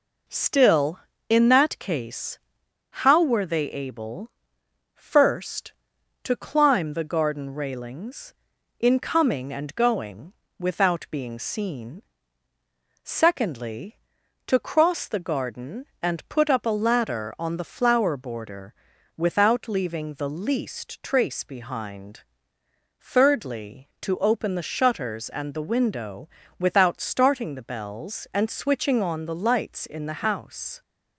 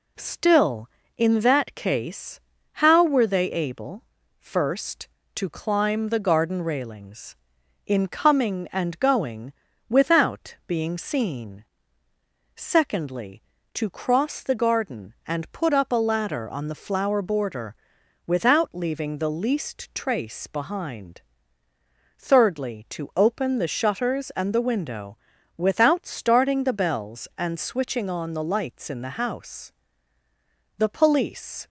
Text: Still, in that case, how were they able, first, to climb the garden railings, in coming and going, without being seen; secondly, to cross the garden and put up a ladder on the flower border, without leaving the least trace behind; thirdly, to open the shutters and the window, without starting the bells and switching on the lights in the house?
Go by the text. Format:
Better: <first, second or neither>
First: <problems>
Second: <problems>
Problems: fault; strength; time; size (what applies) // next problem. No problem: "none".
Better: first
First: none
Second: goes on to say "The police"; noticeable; from 30.7 s on; 0.90 s long